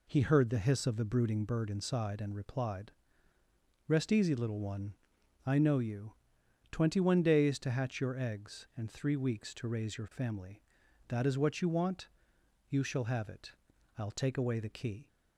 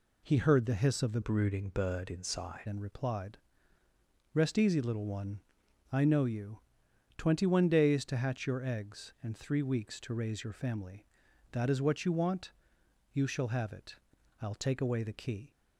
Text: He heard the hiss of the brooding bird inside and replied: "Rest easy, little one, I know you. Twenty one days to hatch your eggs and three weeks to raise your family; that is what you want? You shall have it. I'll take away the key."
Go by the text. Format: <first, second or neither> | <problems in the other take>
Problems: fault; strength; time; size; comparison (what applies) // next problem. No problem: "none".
first | changes voice from "brooding" to "inside"; from 1.2 to 2.6 s; 1.4 s long